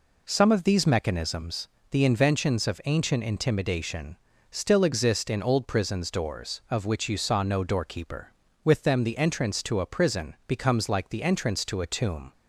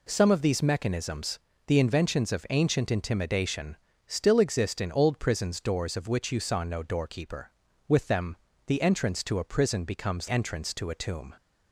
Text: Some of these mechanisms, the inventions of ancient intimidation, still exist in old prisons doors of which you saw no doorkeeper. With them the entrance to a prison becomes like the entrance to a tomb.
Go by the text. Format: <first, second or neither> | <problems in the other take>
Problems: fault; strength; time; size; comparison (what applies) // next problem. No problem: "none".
first | pauses between "them" and "the"; slight; at 8.3 s; 0.30 s long // skips "like the"; at 10.2 s